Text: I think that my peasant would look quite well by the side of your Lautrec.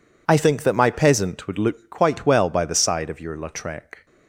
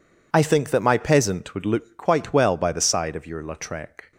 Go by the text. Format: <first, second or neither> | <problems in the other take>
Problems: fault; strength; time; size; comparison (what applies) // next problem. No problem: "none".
neither | none